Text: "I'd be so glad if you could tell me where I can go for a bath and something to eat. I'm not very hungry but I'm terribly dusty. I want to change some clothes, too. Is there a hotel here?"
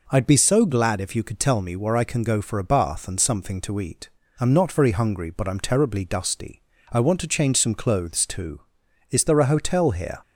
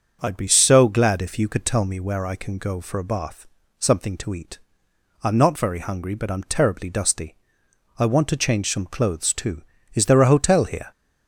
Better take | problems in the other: first | starts louder than the rest; until 1.2 s; 6.5 dB // skips "and"; at 3.6 s

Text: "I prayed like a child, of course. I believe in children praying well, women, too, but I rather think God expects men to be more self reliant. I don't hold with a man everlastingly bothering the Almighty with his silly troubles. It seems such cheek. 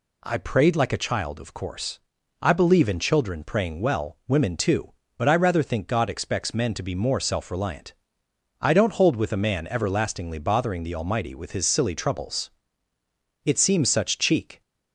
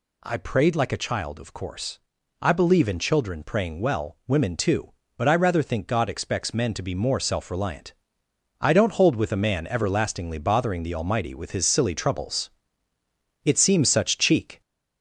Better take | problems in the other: first | gets louder; throughout; 4 dB

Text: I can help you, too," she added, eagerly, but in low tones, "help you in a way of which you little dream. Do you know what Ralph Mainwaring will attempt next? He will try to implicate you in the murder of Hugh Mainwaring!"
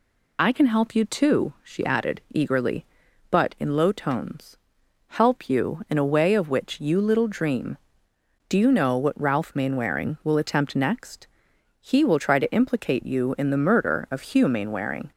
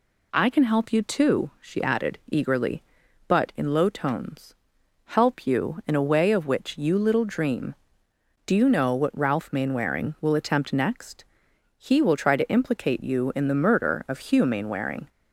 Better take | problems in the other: second | loses the start of "I"; at 0.3 s; 45 ms

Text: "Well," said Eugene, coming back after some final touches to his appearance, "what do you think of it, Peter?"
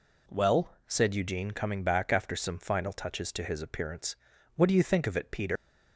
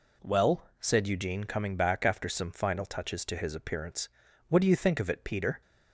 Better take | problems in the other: second | leaves "Peter" unfinished; at 5.5 s; 125 ms

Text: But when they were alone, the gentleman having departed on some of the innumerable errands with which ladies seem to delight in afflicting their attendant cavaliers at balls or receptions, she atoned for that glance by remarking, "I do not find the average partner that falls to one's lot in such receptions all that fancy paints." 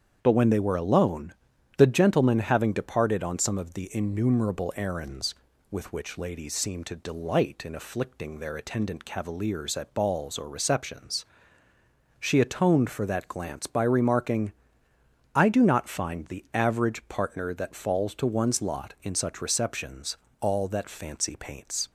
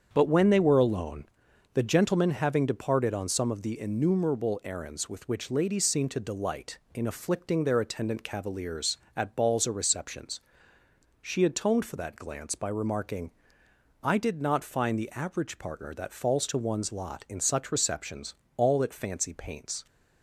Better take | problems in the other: first | starts louder than the rest; strong; until 1.1 s; 7.5 dB; strong in the first // says "did" for "do"; at 14.1 s // pauses between "receptions" and "all"; slight; at 18.3 s; 0.24 s long; slight in the first

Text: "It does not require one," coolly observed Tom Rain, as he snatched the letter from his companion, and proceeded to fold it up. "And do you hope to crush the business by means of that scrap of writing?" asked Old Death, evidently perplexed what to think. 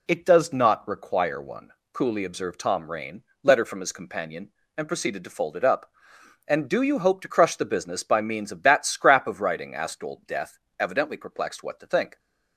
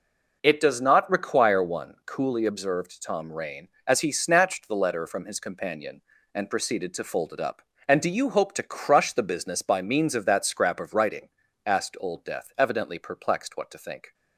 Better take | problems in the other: second | skips "as he snatched the"; at 3.3 s

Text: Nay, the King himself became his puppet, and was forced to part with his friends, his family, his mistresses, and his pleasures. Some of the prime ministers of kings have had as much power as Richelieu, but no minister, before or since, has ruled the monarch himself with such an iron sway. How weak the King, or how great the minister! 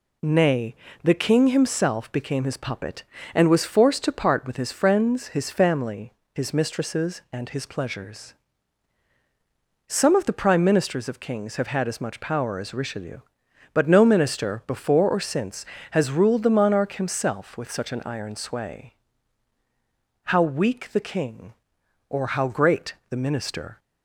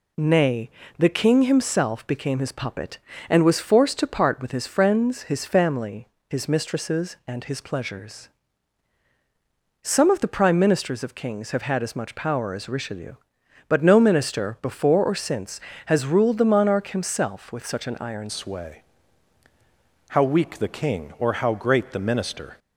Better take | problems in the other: first | changes voice at "sway"; from 18.2 s on; 4.3 s long

